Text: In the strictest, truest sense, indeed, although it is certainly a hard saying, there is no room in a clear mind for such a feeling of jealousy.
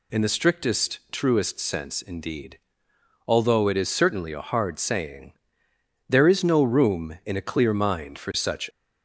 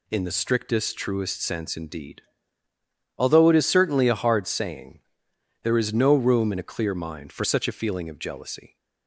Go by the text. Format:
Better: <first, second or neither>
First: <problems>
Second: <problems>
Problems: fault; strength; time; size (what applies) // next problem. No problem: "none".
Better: second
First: stops before "a feeling of jealousy"; at 8.7 s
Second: none